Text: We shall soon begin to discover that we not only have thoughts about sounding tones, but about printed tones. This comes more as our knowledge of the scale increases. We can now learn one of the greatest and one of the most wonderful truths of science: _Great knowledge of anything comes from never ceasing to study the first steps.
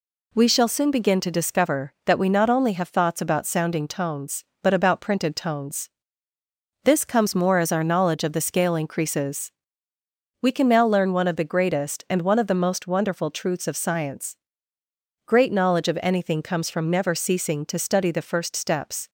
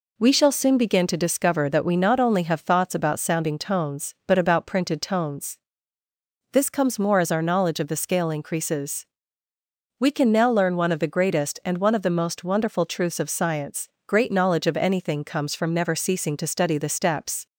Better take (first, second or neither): first